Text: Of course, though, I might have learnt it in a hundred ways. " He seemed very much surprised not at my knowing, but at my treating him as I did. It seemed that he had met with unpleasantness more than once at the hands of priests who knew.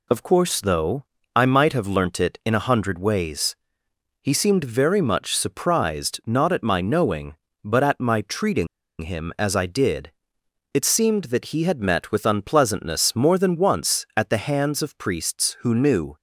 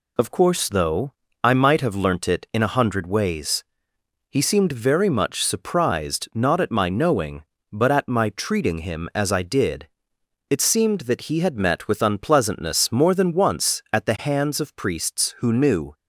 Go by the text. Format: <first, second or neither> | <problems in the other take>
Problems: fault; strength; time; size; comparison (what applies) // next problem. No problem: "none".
second | pauses between "treating" and "him"; slight; at 8.6 s; 0.34 s long